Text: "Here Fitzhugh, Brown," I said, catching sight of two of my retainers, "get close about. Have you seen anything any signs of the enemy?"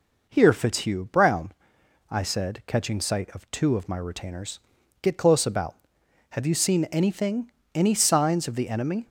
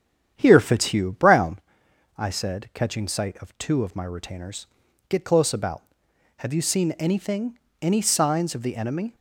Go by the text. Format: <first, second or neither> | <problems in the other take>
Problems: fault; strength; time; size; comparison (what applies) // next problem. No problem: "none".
first | starts louder than the rest; strong; until 1.6 s; 9 dB // pauses between "anything" and "any"; slight; at 7.5 s; 0.24 s long; slight in the first